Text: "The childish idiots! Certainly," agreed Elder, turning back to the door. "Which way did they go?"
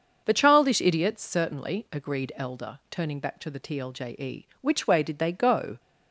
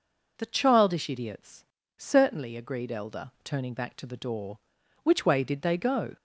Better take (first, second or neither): second